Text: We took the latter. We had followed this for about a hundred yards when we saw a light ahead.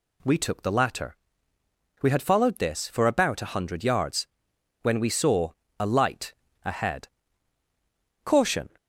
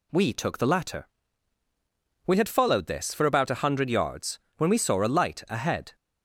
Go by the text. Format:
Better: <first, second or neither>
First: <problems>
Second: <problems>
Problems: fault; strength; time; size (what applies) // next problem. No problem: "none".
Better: second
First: pauses between "yards" and "when"; noticeable; at 4.2 s; 0.56 s long // pauses between "saw" and "a"; slight; at 5.5 s; 0.28 s long // pauses between "light" and "ahead"; slight; at 6.3 s; 0.30 s long // goes on to say "Caution"; slight; from 8.2 s on; 0.44 s long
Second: pauses between "yards" and "when"; slight; at 4.3 s; 0.18 s long